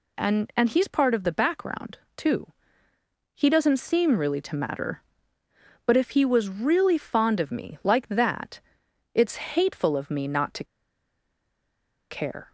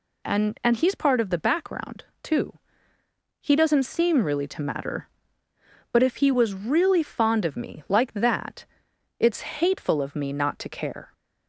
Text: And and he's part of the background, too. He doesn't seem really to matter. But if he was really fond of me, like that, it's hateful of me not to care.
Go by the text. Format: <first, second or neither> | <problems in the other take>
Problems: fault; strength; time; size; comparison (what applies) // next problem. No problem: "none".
second | pauses between "to" and "care"; strong; at 10.6 s; 1.4 s long